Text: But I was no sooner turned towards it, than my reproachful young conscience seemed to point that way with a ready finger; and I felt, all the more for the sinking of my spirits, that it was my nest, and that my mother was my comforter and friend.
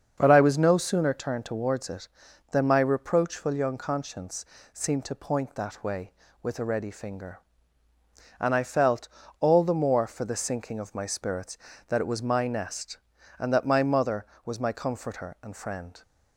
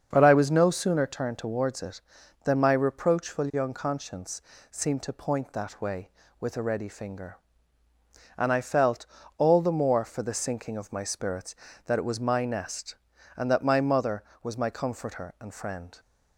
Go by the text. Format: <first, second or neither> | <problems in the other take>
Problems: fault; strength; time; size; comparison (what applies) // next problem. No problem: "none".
neither | starts louder than the rest; the same in both // pauses between "conscience" and "seemed"; slight; the same in both